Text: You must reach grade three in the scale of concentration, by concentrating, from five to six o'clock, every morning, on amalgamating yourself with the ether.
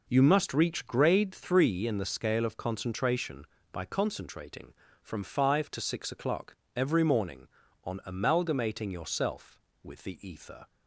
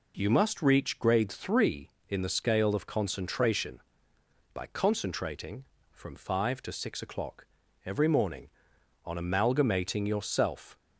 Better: first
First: none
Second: stops before "with the ether"; at 10.7 s

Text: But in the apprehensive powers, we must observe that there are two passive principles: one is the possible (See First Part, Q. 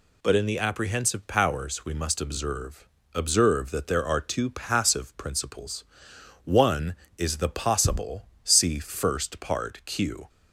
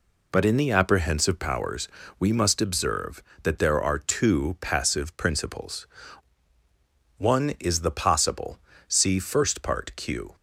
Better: second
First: says "observe" twice; at 3.1 s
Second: none

